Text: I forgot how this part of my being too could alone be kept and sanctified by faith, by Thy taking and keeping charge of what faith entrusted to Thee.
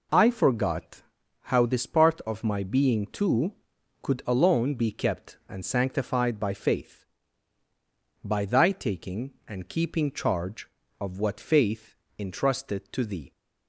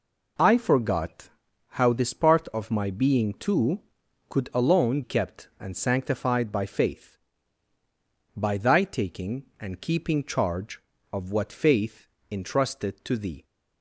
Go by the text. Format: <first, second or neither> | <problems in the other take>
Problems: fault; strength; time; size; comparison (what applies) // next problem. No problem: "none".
first | pauses between "forgot" and "how"; noticeable; at 1.2 s; 0.50 s long; noticeable in the first // skips "be"; at 5.0 s // pauses between "faith" and "entrusted"; slight; at 12.0 s; 0.24 s long; slight in the first